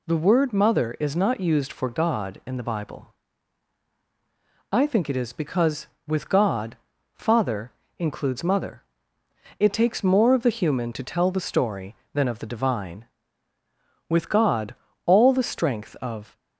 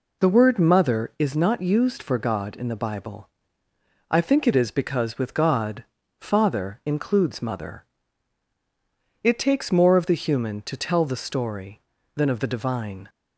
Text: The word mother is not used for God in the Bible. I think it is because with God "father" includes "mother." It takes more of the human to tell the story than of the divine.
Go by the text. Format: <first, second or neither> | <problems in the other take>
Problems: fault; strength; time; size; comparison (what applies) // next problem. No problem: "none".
second | pauses between "God" and "father"; at 6.7 s; 0.40 s long; slight in the second // pauses between "father" and "includes"; slight; at 7.7 s; 0.28 s long // goes on to say "With God all the strength of"; strong; from 14.0 s on; 2.2 s long